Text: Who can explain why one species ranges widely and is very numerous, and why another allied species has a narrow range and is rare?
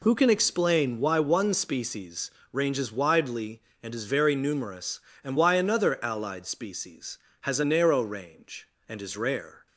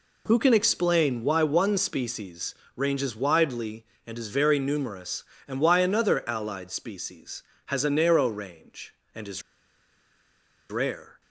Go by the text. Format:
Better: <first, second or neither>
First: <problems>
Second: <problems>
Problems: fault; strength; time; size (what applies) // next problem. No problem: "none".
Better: first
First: pauses between "species" and "ranges"; slight; at 2.3 s; 0.18 s long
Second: pauses between "species" and "ranges"; slight; at 2.5 s; 0.18 s long // pauses between "is" and "rare"; strong; at 9.4 s; 1.3 s long